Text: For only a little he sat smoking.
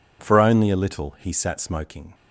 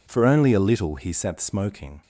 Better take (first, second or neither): neither